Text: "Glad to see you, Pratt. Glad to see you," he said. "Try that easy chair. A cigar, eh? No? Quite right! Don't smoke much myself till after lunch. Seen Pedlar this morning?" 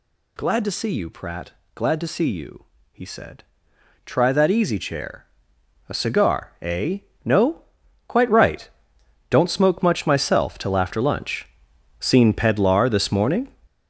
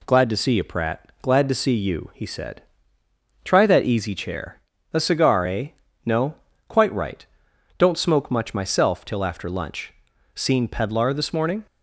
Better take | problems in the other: second | gets louder; strong; throughout; 9.5 dB

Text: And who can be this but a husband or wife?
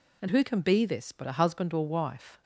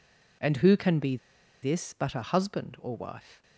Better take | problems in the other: first | pauses between "be" and "this"; at 1.1 s; 0.45 s long

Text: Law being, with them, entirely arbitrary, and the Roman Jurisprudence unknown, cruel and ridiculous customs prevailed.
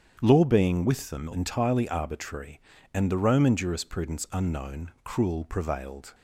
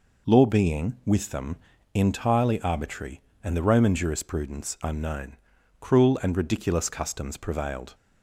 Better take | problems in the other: second | starts louder than the rest; strong; until 1.2 s; 8 dB // skips "and ridiculous customs"; at 5.4 s

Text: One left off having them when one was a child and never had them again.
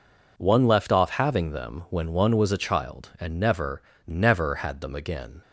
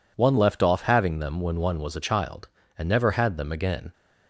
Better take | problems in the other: second | says "never" twice; at 4.0 s

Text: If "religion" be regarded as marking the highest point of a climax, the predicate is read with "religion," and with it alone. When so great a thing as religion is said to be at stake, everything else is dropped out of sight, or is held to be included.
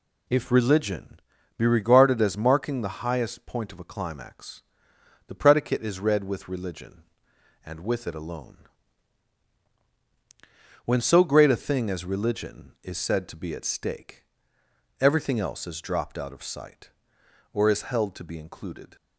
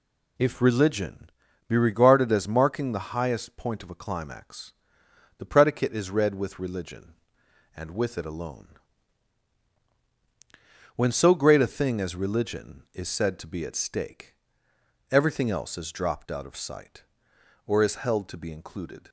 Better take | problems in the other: neither | pauses between "religion" and "be"; slight; the same in both

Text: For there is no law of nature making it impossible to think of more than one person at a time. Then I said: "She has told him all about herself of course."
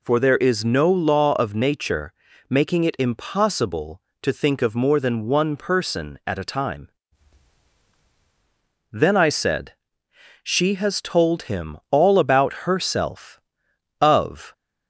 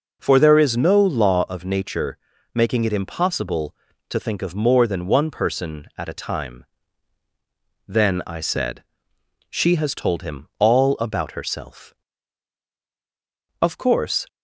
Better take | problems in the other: second | pauses between "nature" and "making"; slight; at 2.1 s; 0.36 s long; slight in the second // pauses between "him" and "all"; slight; at 11.7 s; 0.16 s long // stops before "course"; at 14.5 s

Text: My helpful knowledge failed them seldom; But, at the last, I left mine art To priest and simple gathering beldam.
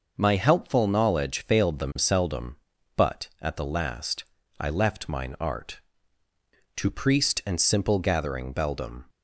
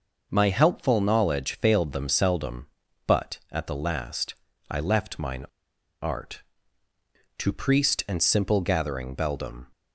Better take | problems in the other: first | pauses between "mine" and "art"; noticeable; at 5.4 s; 0.57 s long

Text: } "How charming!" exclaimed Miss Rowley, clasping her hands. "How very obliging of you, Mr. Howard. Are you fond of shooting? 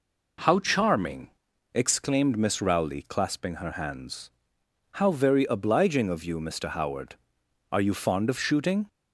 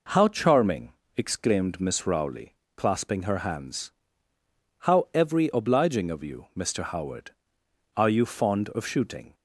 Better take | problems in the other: first | says "every" for "very"; at 5.1 s

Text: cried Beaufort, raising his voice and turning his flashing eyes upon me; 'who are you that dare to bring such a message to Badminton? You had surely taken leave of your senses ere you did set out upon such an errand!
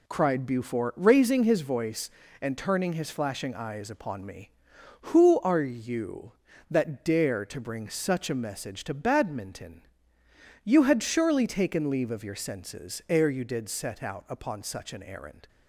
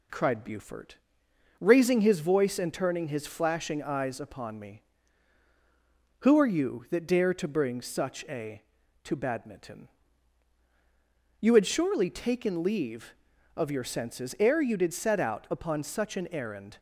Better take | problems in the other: first | skips "message"; at 8.8 s

